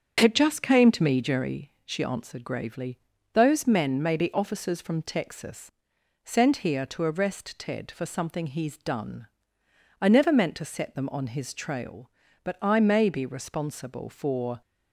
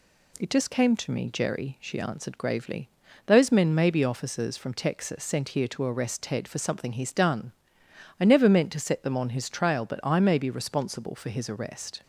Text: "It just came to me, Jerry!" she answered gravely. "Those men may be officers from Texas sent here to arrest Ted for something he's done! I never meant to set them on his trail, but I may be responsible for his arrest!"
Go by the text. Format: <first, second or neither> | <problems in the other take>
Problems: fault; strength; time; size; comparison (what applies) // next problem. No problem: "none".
second | starts louder than the rest; strong; until 1.2 s; 7.5 dB // pauses between "Texas" and "sent"; noticeable; at 5.7 s; 0.54 s long // stops before "his arrest"; at 14.6 s